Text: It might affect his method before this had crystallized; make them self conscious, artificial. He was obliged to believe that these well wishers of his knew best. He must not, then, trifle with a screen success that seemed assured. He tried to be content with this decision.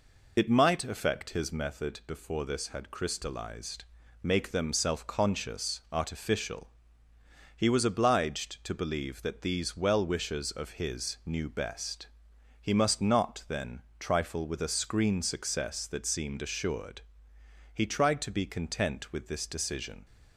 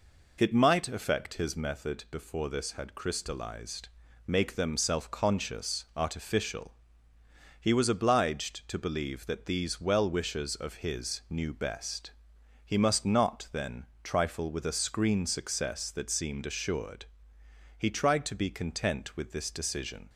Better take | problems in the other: second | loses the start of "It"; at 0.3 s; 25 ms

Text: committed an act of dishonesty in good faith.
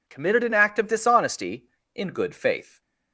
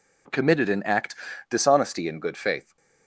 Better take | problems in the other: first | skips "of"; at 1.3 s

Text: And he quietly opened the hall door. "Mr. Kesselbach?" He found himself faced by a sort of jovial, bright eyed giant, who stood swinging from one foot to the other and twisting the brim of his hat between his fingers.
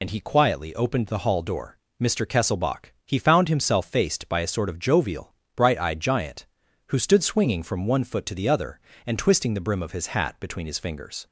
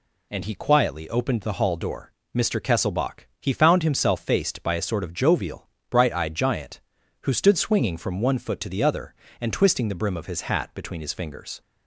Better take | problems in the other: second | loses the start of "And"; at 0.0 s; 50 ms

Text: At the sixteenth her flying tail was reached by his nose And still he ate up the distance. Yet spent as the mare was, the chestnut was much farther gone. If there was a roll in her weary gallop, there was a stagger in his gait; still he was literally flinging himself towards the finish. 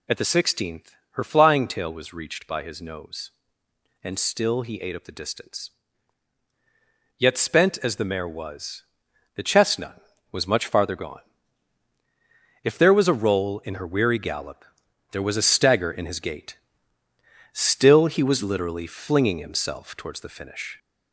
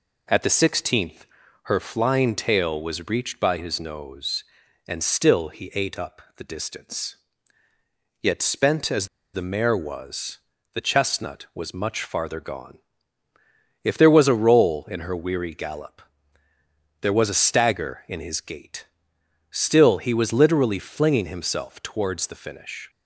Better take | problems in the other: first | pauses between "sixteenth" and "her"; at 1.2 s; 0.38 s long; slight in the first // pauses between "up" and "the"; slight; at 6.1 s; 0.16 s long // pauses between "as" and "the"; slight; at 9.0 s; 0.25 s long

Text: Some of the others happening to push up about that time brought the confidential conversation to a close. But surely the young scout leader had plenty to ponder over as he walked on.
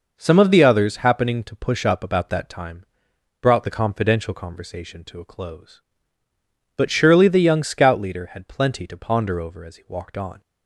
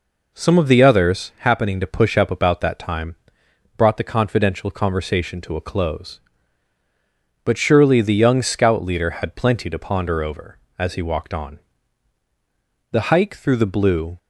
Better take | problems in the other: first | pauses between "time" and "brought"; noticeable; at 3.1 s; 0.64 s long; noticeable in the first // goes on to say "The hike through the Blue"; noticeable; from 12.9 s on; 1.2 s long

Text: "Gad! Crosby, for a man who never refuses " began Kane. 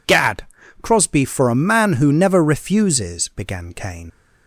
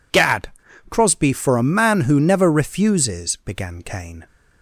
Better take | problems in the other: second | leaves "Kane" unfinished; at 4.0 s; 60 ms

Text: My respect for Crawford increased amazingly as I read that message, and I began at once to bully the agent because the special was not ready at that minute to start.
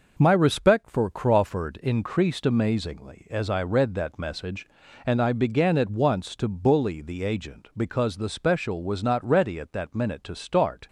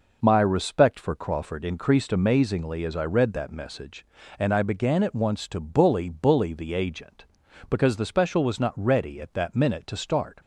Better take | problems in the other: first | says "bully" twice; at 6.0 s

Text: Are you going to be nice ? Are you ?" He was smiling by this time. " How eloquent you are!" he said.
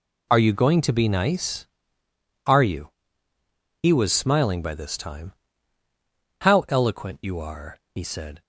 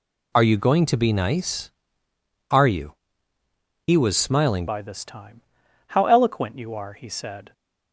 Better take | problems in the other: first | changes voice at "by"; from 4.6 s on; 2.9 s long

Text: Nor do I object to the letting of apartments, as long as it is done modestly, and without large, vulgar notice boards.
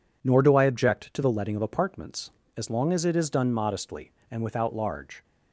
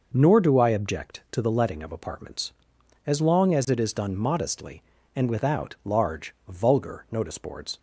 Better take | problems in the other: second | stops before "vulgar notice boards"; at 5.2 s

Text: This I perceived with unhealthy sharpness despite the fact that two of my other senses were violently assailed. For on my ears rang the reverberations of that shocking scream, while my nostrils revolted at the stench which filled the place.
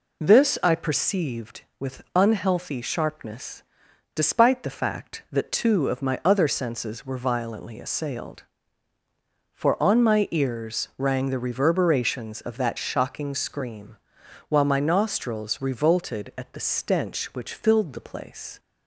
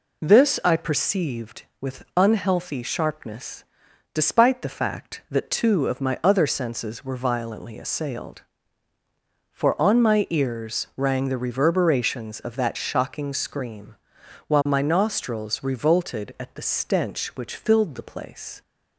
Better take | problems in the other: neither | pauses between "sharpness" and "despite"; noticeable; the same in both

